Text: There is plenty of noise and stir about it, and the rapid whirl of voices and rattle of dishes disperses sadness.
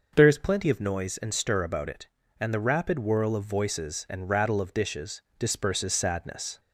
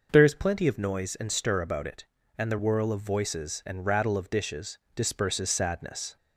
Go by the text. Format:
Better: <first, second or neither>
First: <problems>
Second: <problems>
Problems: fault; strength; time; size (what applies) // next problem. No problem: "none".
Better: first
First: pauses between "dishes" and "disperses"; slight; at 5.2 s; 0.16 s long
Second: skips "rapid"; at 2.5 s // pauses between "dishes" and "disperses"; slight; at 4.7 s; 0.16 s long